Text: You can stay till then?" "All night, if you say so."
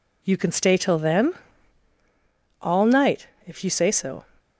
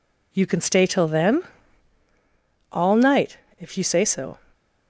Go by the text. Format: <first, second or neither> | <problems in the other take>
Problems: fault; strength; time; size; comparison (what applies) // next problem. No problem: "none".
neither | none